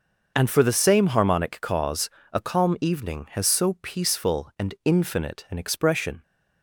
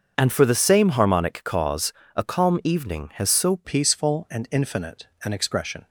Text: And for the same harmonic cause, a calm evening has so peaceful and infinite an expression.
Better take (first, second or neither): first